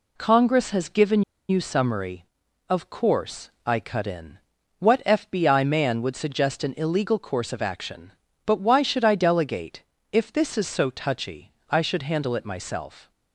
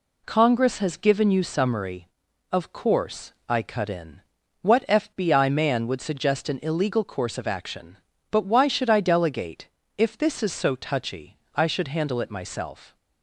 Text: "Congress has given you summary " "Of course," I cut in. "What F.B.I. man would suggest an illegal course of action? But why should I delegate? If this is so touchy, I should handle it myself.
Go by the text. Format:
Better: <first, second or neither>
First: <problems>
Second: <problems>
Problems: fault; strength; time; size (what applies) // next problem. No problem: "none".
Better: second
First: pauses between "given" and "you"; slight; at 1.2 s; 0.27 s long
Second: none